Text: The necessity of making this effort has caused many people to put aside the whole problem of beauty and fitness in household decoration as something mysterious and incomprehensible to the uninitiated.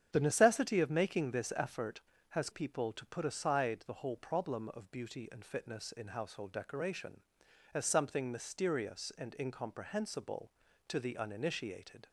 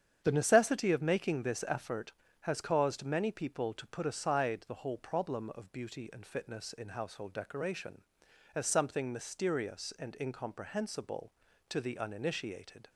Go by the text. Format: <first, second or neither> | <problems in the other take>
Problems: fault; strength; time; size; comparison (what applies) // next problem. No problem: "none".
second | starts louder than the rest; strong; until 1.1 s; 8.5 dB; strong in the second // skips "caused many"; at 2.5 s